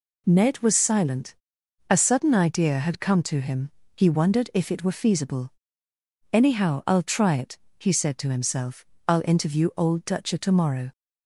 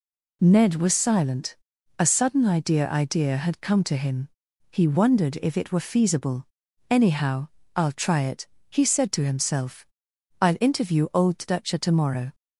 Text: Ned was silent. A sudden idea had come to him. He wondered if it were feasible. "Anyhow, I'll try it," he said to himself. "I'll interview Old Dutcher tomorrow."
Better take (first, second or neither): first